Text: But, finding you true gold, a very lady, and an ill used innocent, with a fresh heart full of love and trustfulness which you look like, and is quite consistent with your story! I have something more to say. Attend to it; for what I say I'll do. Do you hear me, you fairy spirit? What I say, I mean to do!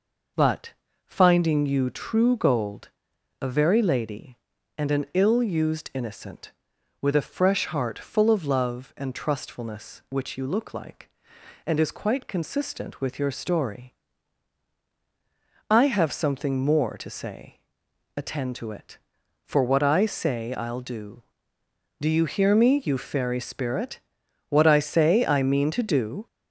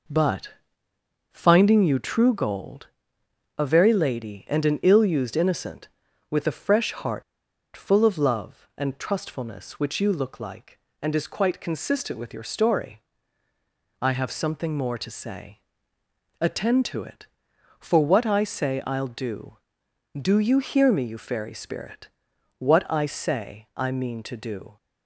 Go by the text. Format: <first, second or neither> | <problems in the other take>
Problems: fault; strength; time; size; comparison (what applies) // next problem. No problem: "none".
first | pauses between "heart" and "full"; noticeable; at 7.2 s; 0.53 s long